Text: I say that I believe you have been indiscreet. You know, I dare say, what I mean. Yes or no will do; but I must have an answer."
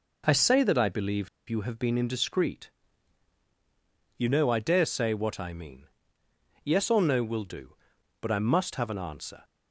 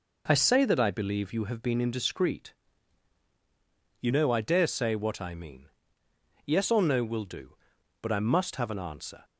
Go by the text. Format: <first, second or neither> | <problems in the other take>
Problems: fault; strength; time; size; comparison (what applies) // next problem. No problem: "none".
second | pauses between "believe" and "you"; slight; at 1.2 s; 0.20 s long